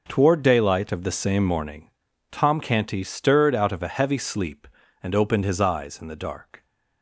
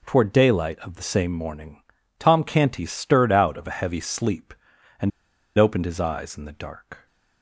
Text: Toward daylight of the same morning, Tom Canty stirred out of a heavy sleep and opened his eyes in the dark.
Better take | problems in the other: first | pauses between "and" and "opened"; noticeable; at 5.1 s; 0.47 s long

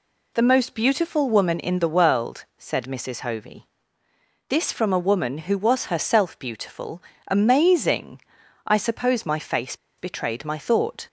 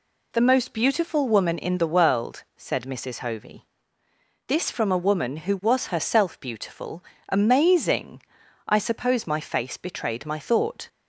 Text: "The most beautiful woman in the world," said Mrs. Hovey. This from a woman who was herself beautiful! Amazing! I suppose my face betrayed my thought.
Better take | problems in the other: second | pauses between "face" and "betrayed"; slight; at 9.7 s; 0.23 s long

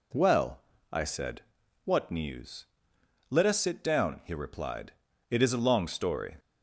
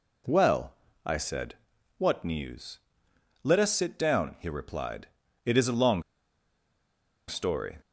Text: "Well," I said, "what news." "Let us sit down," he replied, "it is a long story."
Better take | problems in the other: first | pauses between "long" and "story"; strong; at 6.0 s; 1.2 s long

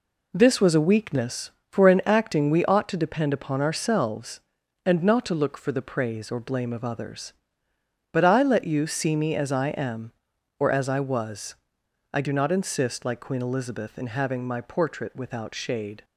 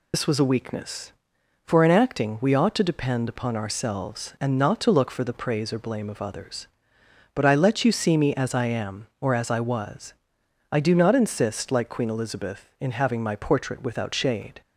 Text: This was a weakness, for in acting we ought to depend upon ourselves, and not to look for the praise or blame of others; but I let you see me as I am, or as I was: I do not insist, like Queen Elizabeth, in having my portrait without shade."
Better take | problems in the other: first | loses the start of "This"; at 0.1 s; 70 ms

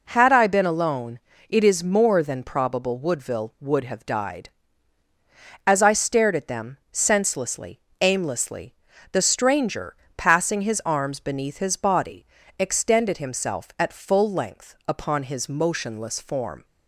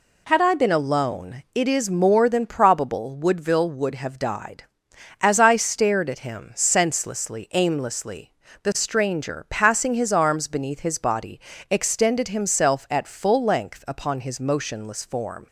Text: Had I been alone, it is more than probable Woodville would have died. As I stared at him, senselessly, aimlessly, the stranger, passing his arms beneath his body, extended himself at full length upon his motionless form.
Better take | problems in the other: second | says "them" for "him"; at 6.4 s

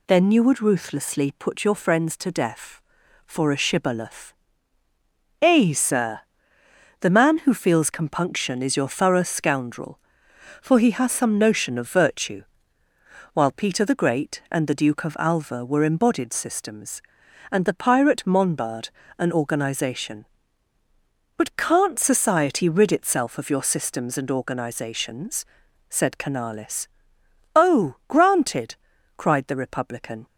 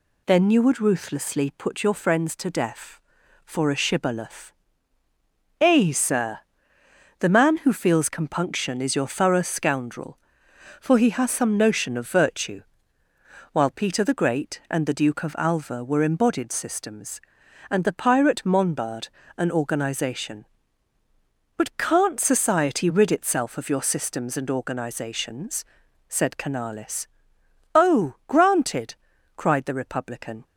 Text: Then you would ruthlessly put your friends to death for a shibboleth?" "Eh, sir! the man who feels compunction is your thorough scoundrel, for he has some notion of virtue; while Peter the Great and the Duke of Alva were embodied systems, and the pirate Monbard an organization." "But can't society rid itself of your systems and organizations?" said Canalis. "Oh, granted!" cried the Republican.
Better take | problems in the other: neither | pauses between "Monbard" and "an"; slight; the same in both

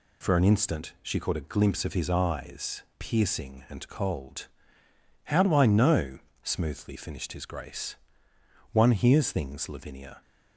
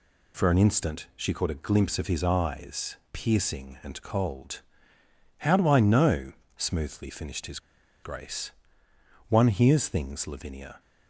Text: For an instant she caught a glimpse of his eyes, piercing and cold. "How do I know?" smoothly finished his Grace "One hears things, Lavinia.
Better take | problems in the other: first | pauses between "his" and "Grace"; at 7.5 s; 0.44 s long // pauses between "Grace" and "One"; noticeable; at 8.5 s; 0.78 s long; noticeable in the first

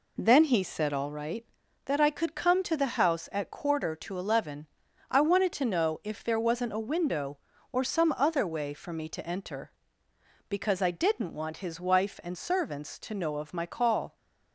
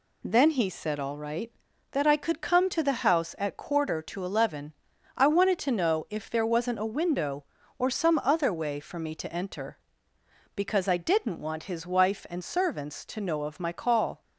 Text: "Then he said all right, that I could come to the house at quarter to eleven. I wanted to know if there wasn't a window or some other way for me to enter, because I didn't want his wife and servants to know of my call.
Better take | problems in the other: second | starts louder than the rest; slight; until 1.2 s; 3 dB

